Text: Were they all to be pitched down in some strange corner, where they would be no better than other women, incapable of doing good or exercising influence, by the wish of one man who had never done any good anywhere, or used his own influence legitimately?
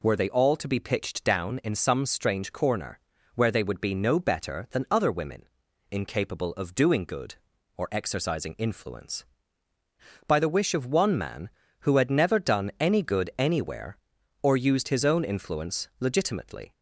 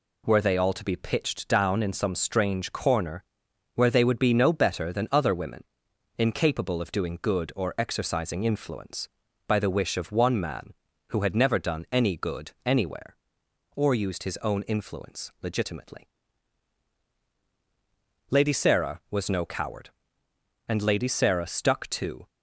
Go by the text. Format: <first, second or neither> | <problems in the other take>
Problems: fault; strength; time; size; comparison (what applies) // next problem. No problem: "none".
first | goes on to say "Lady Sarah was no coward and Lady Sarah stuck to"; strong; from 18.3 s on; 3.9 s long